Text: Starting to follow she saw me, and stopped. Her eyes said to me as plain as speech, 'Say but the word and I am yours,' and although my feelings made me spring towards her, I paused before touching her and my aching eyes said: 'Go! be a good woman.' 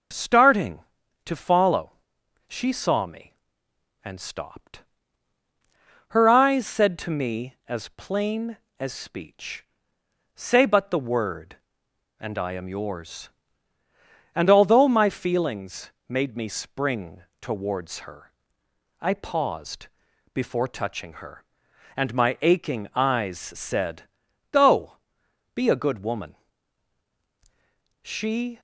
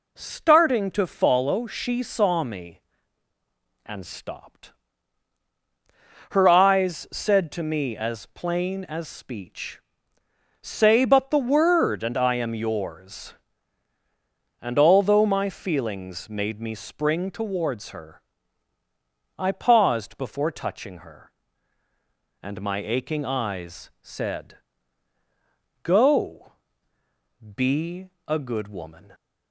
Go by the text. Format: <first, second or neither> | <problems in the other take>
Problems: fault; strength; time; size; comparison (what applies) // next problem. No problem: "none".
second | pauses between "follow" and "she"; noticeable; at 1.9 s; 0.54 s long // pauses between "feelings" and "made"; slight; at 15.9 s; 0.18 s long // pauses between "spring" and "towards"; slight; at 17.2 s; 0.18 s long // pauses between "paused" and "before"; noticeable; at 19.8 s; 0.46 s long // goes on to say "She"; from 28.0 s on; 0.58 s long